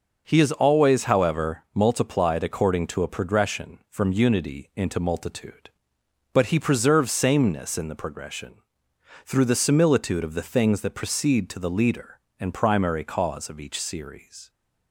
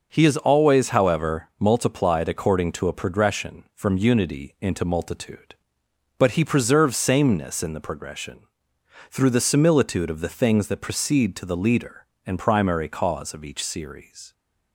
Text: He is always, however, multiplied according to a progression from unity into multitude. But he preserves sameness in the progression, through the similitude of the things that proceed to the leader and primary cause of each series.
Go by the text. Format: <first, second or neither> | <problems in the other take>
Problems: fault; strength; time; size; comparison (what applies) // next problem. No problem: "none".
neither | none